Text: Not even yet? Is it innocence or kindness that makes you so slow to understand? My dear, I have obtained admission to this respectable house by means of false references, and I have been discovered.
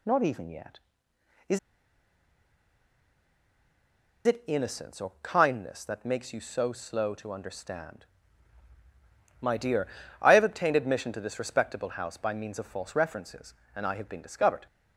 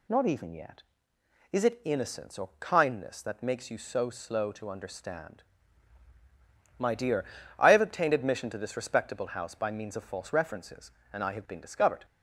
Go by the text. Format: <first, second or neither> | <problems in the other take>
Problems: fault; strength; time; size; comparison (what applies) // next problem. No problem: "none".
second | pauses between "Is" and "it"; strong; at 1.5 s; 2.6 s long